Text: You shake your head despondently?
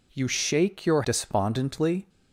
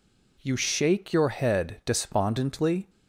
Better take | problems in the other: second | skips "head"; at 1.0 s

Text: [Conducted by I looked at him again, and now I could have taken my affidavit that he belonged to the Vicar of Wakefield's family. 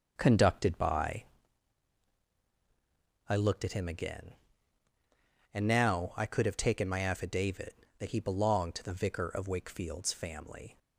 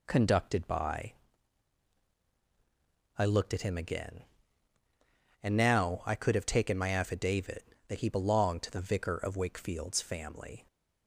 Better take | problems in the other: second | starts louder than the rest; noticeable; until 1.6 s; 6 dB // pauses between "by" and "I"; strong; at 1.2 s; 2.0 s long; strong in the second

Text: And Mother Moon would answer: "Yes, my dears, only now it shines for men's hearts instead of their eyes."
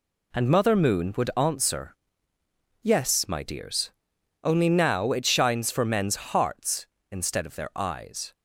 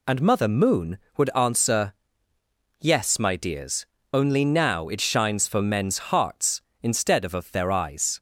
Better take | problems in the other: first | says "of" twice; at 7.3 s

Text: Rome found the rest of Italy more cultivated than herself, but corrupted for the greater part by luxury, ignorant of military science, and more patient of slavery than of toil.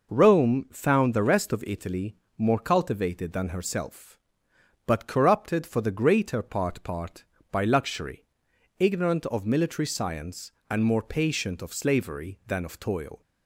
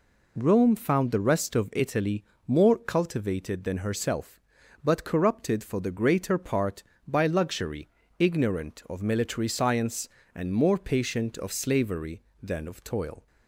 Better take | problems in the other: second | pauses between "Italy" and "more"; slight; at 2.1 s; 0.22 s long; slight in the second // says "part" twice; at 6.8 s

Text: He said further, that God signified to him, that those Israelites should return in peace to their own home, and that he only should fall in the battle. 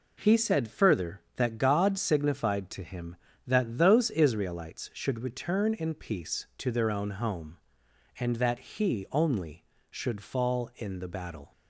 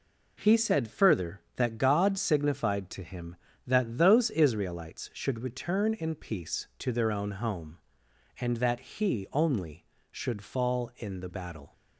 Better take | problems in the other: neither | none

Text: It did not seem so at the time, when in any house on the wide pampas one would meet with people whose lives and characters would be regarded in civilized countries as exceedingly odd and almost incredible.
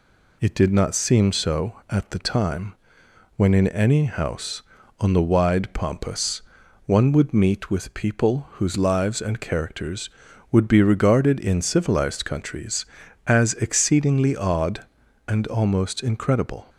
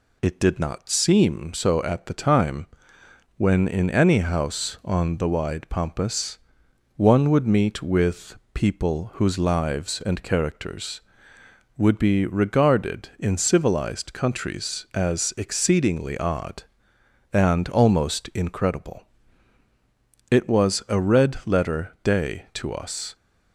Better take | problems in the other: first | pauses between "pampas" and "one"; noticeable; at 6.3 s; 0.58 s long; also in the first // pauses between "with" and "people"; slight; at 8.3 s; 0.16 s long // goes on to say "It was a red letter day to us"; strong; from 20.2 s on; 2.8 s long

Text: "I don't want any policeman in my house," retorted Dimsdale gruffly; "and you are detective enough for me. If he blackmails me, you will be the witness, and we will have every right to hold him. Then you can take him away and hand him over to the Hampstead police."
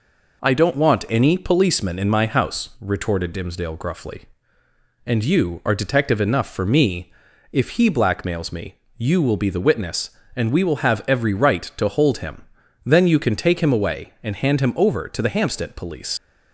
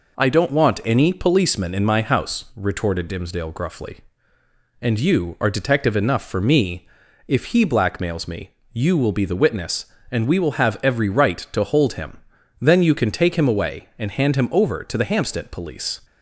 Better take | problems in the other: second | leaves "police" unfinished; at 16.1 s; 120 ms

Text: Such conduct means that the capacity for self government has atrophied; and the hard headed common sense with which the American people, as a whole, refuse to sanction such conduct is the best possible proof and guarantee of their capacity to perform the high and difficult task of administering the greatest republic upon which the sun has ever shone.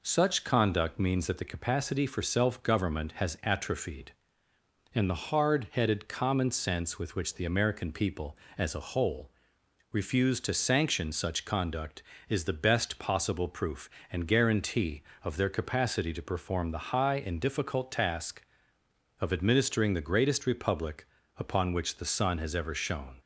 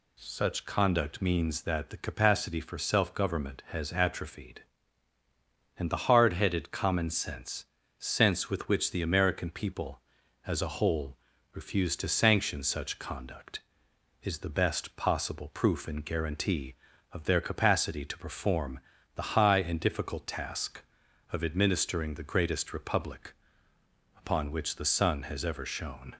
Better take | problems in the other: first | says "sense" twice; at 7.9 s // pauses between "perform" and "the"; slight; at 18.7 s; 0.34 s long // pauses between "republic" and "upon"; noticeable; at 23.3 s; 0.82 s long; slight in the first

